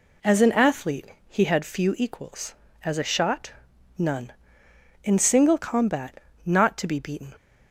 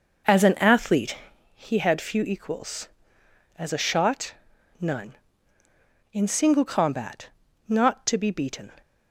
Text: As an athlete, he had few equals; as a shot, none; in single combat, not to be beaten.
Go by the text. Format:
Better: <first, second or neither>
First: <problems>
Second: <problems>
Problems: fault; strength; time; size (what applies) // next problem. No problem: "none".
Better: first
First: none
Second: starts louder than the rest; noticeable; until 1.4 s; 5.5 dB